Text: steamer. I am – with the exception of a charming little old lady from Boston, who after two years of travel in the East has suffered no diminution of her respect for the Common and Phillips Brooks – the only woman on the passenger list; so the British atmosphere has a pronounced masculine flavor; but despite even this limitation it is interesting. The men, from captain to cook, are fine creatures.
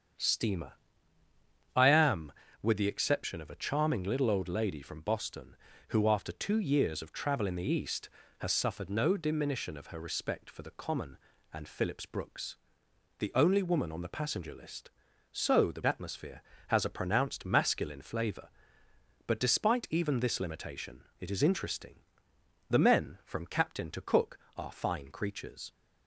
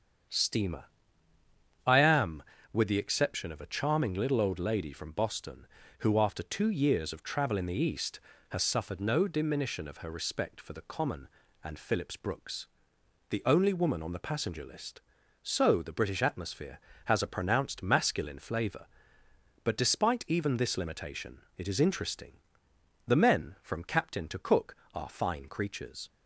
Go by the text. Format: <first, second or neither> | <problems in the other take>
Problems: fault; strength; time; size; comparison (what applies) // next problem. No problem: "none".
second | starts louder than the rest; strong; until 2.2 s; 8 dB; strong in the second // skips "British"; at 15.8 s // pauses between "limitation" and "it"; slight; at 21.0 s; 0.16 s long; slight in the second